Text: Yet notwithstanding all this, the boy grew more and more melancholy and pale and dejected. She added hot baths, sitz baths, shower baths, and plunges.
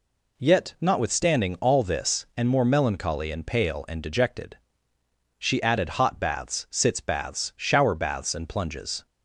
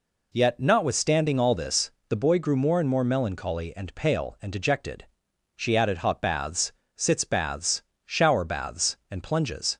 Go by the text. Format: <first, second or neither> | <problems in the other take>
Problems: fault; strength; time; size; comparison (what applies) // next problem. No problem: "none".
second | skips "the boy grew more"; at 2.3 s